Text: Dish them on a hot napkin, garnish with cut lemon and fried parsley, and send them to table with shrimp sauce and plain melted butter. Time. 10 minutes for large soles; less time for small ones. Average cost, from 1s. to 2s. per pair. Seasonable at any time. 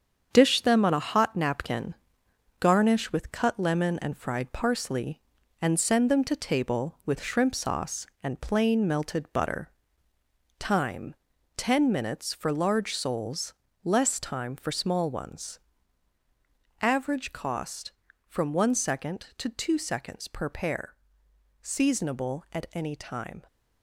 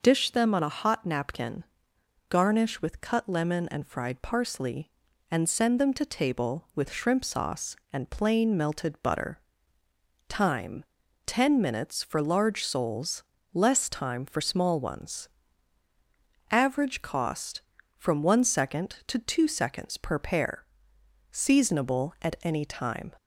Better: second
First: gets quieter; throughout; 6.5 dB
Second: none

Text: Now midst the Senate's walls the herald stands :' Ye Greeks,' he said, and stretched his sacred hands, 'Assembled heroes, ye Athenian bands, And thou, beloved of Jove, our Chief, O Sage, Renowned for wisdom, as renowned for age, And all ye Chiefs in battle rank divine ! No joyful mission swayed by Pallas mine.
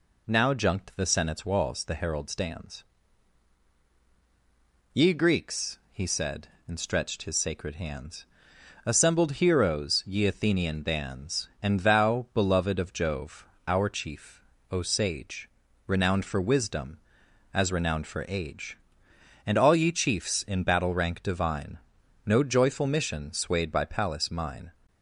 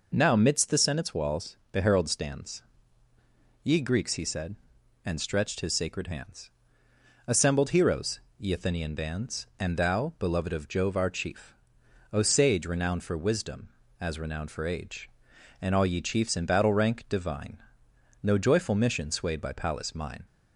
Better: second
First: says "junked" for "midst"; at 0.5 s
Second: none

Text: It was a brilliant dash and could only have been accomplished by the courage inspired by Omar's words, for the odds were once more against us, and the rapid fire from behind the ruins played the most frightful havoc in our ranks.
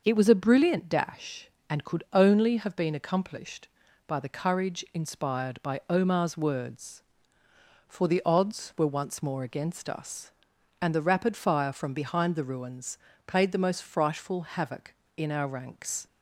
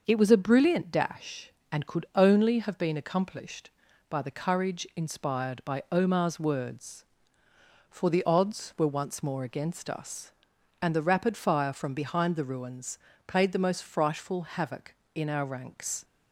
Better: neither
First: starts louder than the rest; noticeable; until 1.0 s; 6 dB // pauses between "ruins" and "played"; slight; at 12.9 s; 0.28 s long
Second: starts louder than the rest; noticeable; until 1.0 s; 6 dB // pauses between "ruins" and "played"; slight; at 12.9 s; 0.28 s long

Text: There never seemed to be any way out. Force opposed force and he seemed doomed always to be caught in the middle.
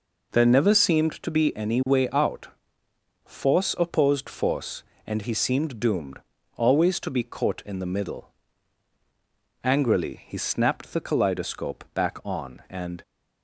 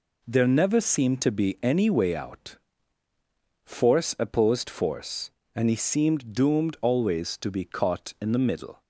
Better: second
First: pauses between "doomed" and "always"; slight; at 6.2 s; 0.36 s long // goes on to say "Angrily he snapped the kaleidoscope back on and"; strong; from 9.6 s on; 3.3 s long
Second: none

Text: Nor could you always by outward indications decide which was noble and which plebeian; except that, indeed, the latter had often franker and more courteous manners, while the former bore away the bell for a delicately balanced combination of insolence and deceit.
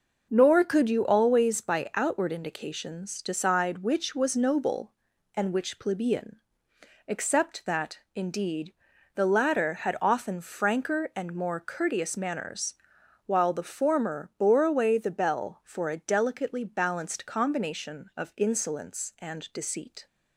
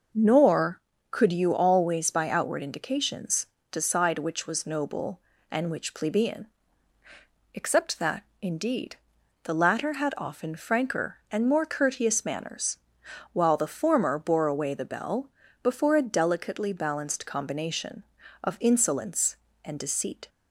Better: first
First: none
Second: pauses between "indications" and "decide"; slight; at 3.4 s; 0.24 s long // says "before" for "for"; at 15.6 s

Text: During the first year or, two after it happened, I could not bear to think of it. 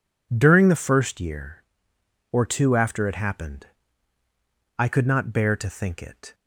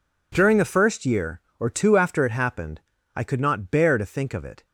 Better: second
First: skips "of"; at 6.0 s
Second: none

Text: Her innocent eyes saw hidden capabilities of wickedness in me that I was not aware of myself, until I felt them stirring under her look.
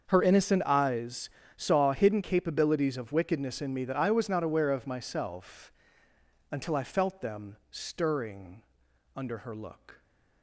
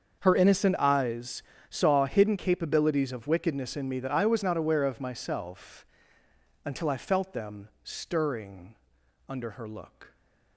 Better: neither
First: starts louder than the rest; until 1.1 s; 7 dB // pauses between "eyes" and "saw"; slight; at 1.2 s; 0.28 s long // pauses between "them" and "stirring"; slight; at 7.5 s; 0.15 s long // pauses between "stirring" and "under"; noticeable; at 8.6 s; 0.52 s long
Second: starts louder than the rest; until 1.2 s; 7 dB // pauses between "eyes" and "saw"; slight; at 1.4 s; 0.28 s long // pauses between "them" and "stirring"; slight; at 7.6 s; 0.16 s long // pauses between "stirring" and "under"; noticeable; at 8.7 s; 0.52 s long

